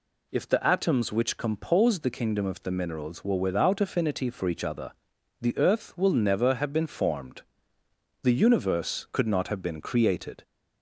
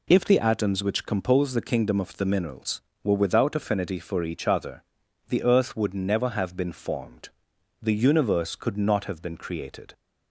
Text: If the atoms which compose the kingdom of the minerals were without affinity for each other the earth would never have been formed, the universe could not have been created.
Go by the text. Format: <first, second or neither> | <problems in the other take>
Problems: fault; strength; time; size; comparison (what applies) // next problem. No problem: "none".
second | pauses between "other" and "the"; noticeable; at 4.9 s; 0.48 s long; noticeable in the second // says "will" for "would"; at 5.9 s